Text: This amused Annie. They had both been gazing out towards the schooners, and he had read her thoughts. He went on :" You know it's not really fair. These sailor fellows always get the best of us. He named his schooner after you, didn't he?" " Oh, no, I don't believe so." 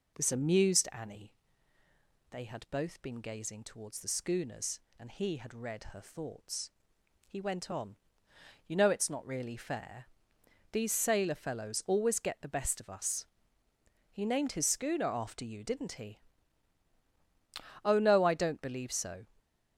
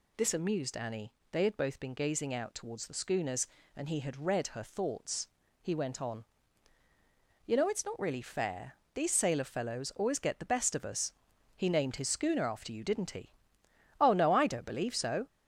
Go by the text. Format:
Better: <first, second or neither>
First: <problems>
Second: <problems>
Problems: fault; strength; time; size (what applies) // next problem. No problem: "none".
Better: second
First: skips "out"; at 3.6 s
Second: none